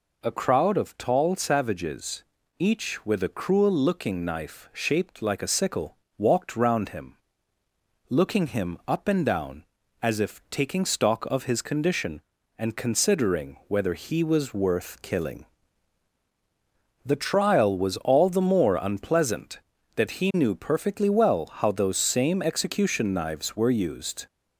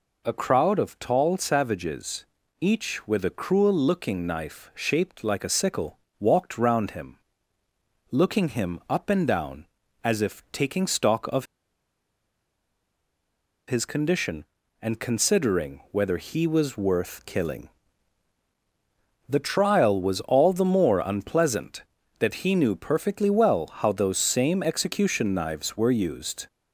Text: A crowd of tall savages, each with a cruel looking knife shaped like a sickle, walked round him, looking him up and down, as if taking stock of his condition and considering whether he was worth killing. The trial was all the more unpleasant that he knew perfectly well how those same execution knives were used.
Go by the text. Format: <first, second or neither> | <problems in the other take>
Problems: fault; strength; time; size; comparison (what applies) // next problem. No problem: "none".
first | pauses between "of" and "his"; strong; at 11.4 s; 2.2 s long